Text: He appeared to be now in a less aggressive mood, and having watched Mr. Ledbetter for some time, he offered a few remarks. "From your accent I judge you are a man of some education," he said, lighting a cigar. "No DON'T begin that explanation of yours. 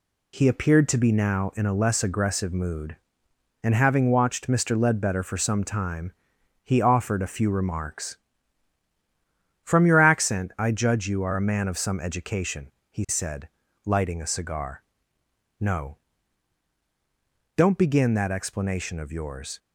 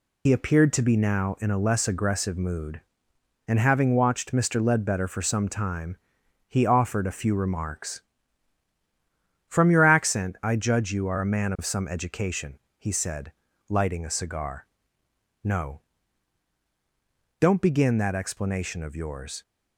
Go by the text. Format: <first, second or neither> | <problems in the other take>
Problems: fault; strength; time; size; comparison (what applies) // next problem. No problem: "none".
first | loses the start of "He"; at 0.2 s; 75 ms // pauses between "No" and "DON'T"; strong; at 15.7 s; 1.6 s long; strong in the first